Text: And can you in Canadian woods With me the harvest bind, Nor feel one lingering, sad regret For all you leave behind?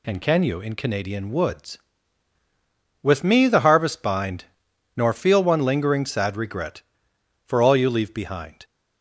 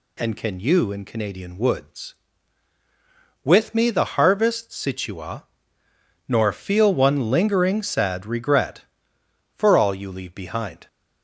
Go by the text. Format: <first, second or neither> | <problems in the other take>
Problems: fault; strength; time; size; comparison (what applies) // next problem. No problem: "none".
first | says "situa" for "bind"; at 4.7 s